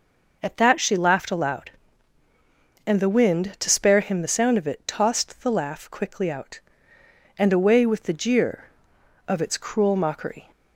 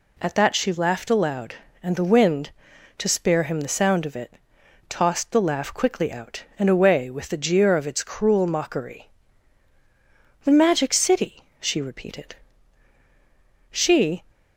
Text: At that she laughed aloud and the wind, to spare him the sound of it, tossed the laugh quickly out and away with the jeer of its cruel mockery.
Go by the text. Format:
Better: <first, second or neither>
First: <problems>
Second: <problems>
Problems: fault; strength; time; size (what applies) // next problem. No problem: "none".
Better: first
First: none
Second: goes on to say "The Magic City she repeated She"; strong; from 10.4 s on; 3.8 s long